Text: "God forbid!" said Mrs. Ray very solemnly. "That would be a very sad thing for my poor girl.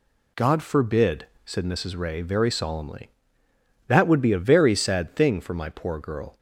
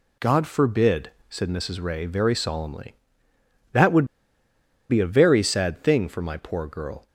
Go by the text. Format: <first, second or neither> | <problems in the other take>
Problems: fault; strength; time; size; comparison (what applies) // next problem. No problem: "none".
first | pauses between "would" and "be"; noticeable; at 4.0 s; 0.85 s long